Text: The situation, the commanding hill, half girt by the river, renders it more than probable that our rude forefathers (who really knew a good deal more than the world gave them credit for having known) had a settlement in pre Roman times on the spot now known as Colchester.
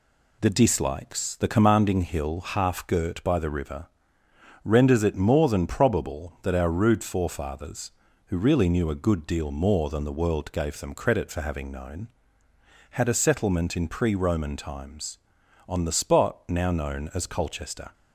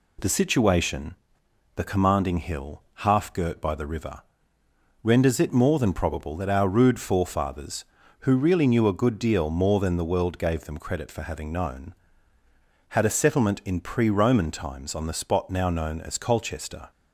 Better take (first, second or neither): second